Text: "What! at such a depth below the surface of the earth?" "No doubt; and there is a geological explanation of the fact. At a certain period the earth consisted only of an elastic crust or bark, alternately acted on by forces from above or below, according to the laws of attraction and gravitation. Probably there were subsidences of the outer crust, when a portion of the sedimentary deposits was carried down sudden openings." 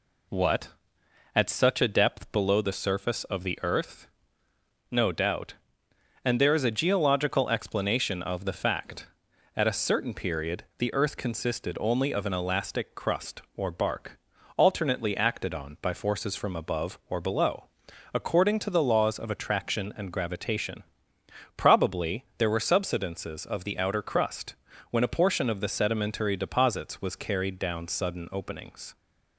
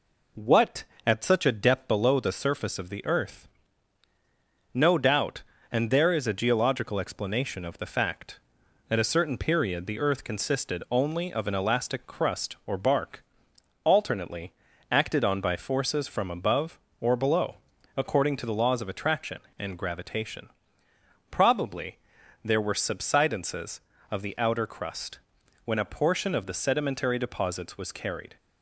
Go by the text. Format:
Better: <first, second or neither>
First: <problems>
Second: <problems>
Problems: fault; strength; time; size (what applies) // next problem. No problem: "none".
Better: first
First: none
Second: pauses between "alternately" and "acted"; at 14.5 s; 0.38 s long // pauses between "Probably" and "there"; noticeable; at 21.9 s; 0.48 s long // stops before "down sudden openings"; at 28.3 s